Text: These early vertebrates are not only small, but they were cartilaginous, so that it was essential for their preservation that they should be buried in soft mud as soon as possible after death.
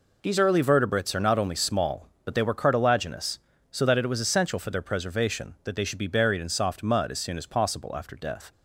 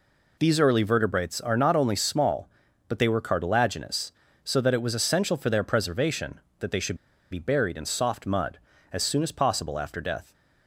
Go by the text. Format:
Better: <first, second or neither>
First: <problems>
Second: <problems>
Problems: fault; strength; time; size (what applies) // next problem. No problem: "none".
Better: first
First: none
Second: pauses between "should" and "be"; slight; at 6.9 s; 0.34 s long